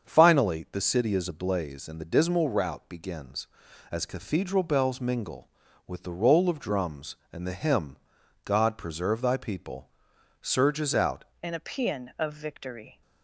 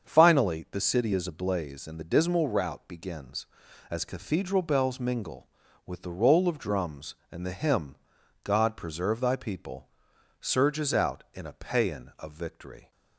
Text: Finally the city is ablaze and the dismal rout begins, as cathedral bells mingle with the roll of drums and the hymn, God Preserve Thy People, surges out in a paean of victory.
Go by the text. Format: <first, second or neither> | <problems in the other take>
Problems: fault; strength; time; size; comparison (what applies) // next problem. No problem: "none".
second | starts louder than the rest; until 1.1 s; 7 dB; also in the second // changes voice at "in"; from 11.4 s on; 1.6 s long